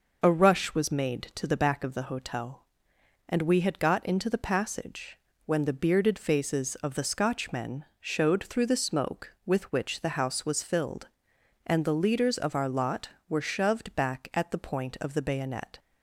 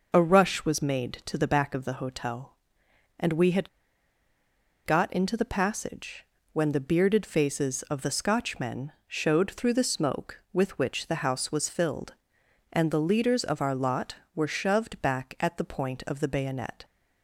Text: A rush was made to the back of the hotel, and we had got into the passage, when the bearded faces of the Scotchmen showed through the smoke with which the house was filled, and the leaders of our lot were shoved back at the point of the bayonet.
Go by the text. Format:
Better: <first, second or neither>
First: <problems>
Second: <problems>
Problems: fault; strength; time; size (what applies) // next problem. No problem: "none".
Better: first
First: none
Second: pauses between "had" and "got"; at 3.6 s; 1.1 s long